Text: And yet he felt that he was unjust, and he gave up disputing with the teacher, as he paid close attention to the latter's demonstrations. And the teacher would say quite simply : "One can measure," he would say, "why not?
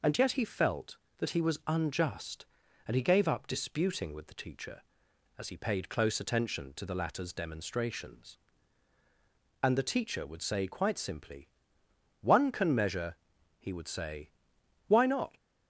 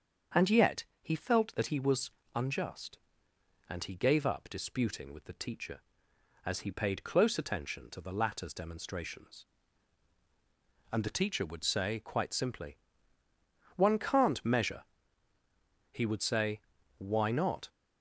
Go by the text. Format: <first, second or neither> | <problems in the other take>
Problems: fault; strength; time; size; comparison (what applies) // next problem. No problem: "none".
first | starts louder than the rest; strong; until 1.5 s; 7 dB // pauses between "yet" and "he"; slight; at 0.8 s; 0.18 s long // pauses between "was" and "unjust"; slight; at 2.1 s; 0.24 s long // says "can't" for "can"; at 13.9 s